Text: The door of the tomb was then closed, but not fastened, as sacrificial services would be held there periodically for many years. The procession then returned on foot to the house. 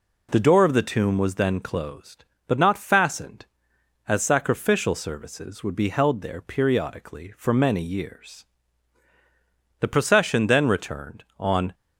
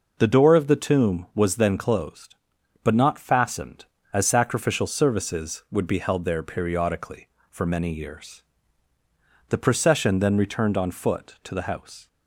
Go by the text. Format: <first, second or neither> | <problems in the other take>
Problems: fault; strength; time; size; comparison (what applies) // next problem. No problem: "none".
second | stops before "foot to the house"; at 11.7 s